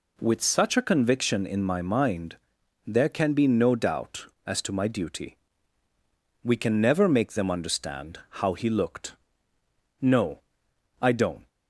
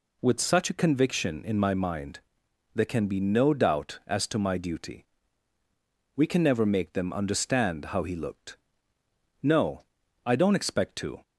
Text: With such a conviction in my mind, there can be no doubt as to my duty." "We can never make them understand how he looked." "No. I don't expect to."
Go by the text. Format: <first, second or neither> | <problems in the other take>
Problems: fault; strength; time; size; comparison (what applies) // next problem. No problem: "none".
second | pauses between "understand" and "how"; slight; at 8.1 s; 0.24 s long // stops before "expect to"; at 11.4 s